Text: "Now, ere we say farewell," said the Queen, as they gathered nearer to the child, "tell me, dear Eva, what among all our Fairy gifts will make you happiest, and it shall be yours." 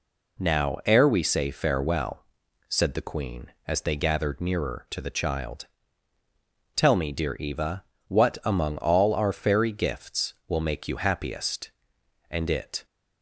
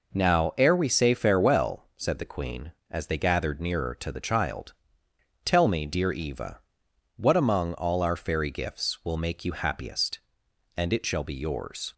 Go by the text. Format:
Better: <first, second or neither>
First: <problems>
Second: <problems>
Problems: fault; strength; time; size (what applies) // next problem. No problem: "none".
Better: second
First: stops before "shall be yours"; at 12.8 s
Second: none